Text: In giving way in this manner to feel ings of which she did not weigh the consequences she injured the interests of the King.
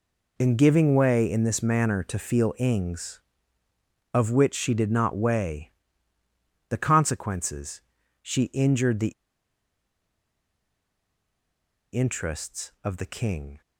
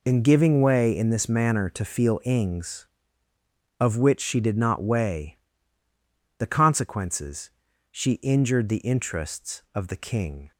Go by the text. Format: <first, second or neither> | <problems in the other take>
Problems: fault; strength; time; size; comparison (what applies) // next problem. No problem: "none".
second | pauses between "weigh" and "the"; noticeable; at 5.7 s; 0.96 s long; also in the second // pauses between "consequences" and "she"; at 7.8 s; 0.40 s long; also in the second // pauses between "the" and "interests"; strong; at 9.1 s; 2.8 s long